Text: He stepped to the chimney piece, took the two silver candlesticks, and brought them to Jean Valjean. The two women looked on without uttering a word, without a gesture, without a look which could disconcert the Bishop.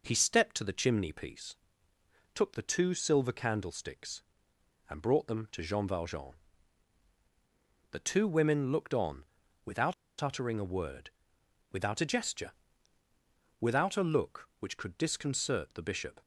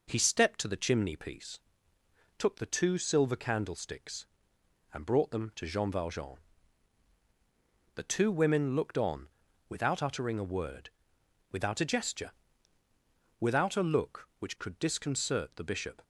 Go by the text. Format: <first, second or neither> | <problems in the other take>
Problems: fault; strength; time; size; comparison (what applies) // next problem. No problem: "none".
second | pauses between "on" and "without"; at 9.2 s; 0.40 s long; also in the second // pauses between "without" and "uttering"; slight; at 9.9 s; 0.27 s long